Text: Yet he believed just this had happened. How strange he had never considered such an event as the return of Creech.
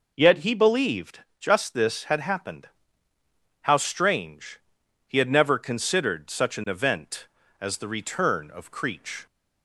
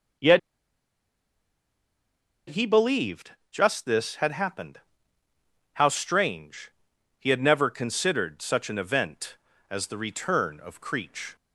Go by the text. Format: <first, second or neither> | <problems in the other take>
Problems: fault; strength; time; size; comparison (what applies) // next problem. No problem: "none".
first | pauses between "Yet" and "he"; strong; at 0.3 s; 2.0 s long // pauses between "believed" and "just"; slight; at 3.3 s; 0.20 s long; slight in the first // pauses between "strange" and "he"; noticeable; at 6.7 s; 0.48 s long; noticeable in the first